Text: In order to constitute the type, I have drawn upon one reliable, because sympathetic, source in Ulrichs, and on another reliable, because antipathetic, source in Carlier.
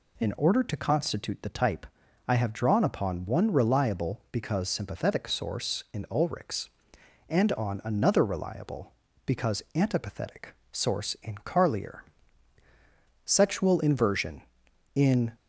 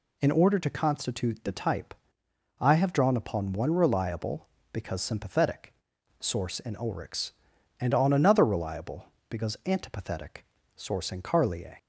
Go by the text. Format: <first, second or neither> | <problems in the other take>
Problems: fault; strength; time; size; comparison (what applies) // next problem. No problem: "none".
second | goes on to say "Sexual inversion in"; strong; from 13.2 s on; 2.0 s long